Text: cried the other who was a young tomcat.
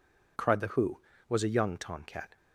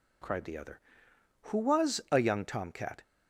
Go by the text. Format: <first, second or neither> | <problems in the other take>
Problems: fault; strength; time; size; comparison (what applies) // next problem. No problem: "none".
second | skips "other"; at 0.6 s